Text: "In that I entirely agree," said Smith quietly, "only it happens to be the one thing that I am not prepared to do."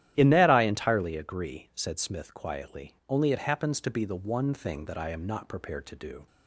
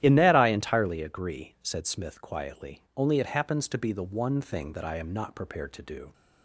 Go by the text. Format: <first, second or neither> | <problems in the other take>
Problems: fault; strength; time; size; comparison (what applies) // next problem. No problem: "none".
neither | starts louder than the rest; strong; the same in both